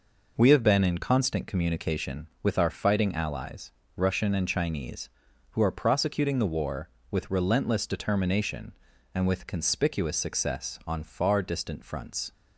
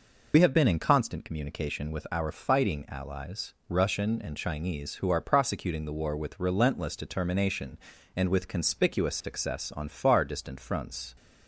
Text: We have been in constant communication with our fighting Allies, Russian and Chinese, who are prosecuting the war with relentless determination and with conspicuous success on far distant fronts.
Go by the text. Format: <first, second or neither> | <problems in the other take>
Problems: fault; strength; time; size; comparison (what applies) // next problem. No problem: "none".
first | loses the start of "We"; at 0.3 s; 50 ms